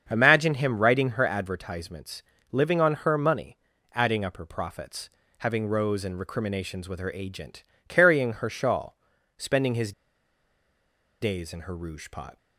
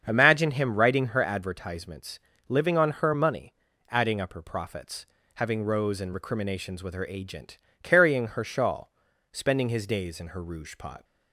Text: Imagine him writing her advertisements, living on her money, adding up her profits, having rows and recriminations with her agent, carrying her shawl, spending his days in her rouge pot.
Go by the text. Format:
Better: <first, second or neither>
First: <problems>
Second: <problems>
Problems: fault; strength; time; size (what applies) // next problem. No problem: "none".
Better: second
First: starts louder than the rest; strong; until 1.1 s; 7 dB // pauses between "his" and "days"; strong; at 9.9 s; 1.3 s long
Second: starts louder than the rest; strong; until 1.0 s; 7 dB